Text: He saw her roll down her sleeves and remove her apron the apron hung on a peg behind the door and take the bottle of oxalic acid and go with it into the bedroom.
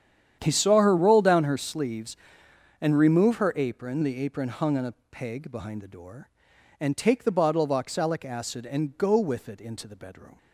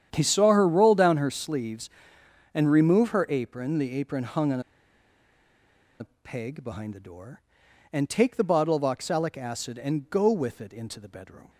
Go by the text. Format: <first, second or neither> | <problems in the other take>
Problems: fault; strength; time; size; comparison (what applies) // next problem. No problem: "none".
first | starts louder than the rest; strong; until 1.1 s; 9 dB; strong in the first // pauses between "on" and "a"; strong; at 4.6 s; 1.3 s long // pauses between "a" and "peg"; slight; at 6.0 s; 0.18 s long; slight in the first